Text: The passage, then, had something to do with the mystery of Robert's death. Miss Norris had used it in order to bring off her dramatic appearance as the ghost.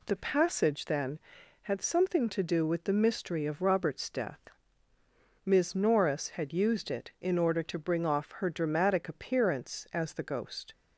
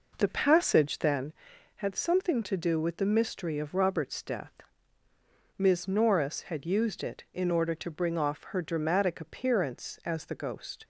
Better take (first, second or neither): first